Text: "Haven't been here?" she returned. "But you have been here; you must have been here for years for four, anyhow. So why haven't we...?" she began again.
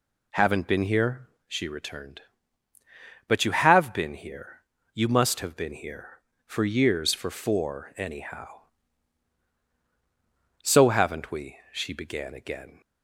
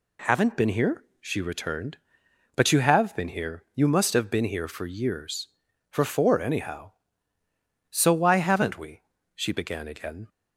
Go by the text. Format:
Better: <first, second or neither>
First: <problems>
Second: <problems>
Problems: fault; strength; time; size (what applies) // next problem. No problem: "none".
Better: second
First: skips "why"; at 10.9 s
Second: none